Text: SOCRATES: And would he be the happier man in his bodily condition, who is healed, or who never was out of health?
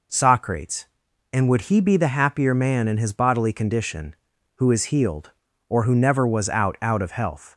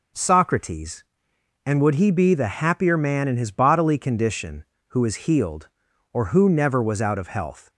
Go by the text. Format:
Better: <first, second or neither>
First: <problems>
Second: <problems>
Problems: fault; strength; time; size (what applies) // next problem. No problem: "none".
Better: second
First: says "out" twice; at 6.8 s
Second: none